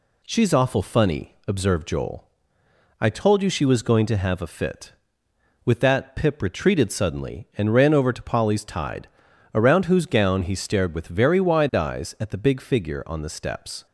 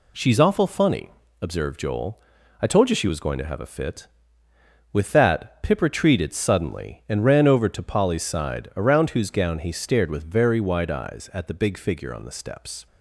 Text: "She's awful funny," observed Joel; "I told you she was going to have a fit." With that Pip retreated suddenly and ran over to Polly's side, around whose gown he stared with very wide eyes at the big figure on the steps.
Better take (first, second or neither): second